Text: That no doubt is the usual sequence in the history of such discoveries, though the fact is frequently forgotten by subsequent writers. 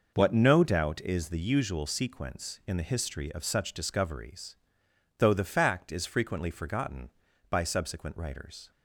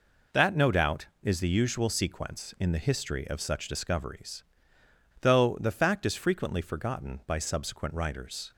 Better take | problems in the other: second | says "What" for "That"; at 0.1 s

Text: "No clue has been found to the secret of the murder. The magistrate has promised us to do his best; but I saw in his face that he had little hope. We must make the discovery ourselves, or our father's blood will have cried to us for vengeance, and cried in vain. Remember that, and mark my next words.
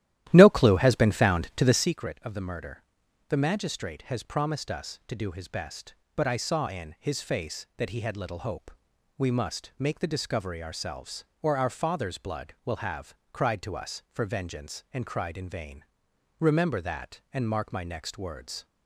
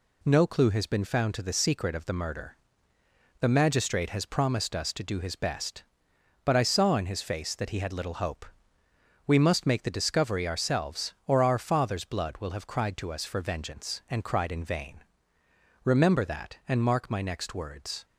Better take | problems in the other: second | starts louder than the rest; strong; until 1.9 s; 13 dB // pauses between "have" and "cried"; slight; at 13.1 s; 0.18 s long

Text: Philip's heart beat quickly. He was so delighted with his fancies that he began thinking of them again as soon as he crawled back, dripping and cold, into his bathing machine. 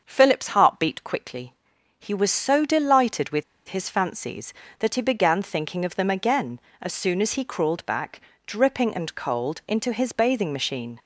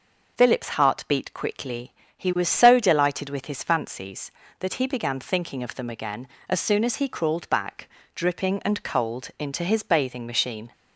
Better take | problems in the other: second | starts louder than the rest; until 1.0 s; 6.5 dB // pauses between "with" and "his"; slight; at 3.4 s; 0.25 s long

